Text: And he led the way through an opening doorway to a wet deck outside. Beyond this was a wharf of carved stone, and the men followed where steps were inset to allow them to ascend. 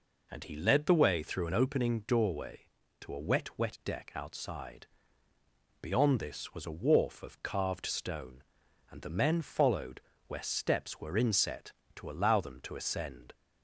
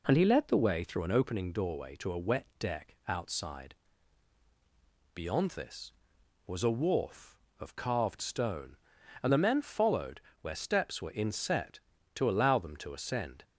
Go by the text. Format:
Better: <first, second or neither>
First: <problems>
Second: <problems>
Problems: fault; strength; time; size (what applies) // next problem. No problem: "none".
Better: second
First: says "wet" twice; at 3.5 s // pauses between "followed" and "where"; slight; at 9.9 s; 0.28 s long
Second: pauses between "followed" and "where"; slight; at 10.1 s; 0.22 s long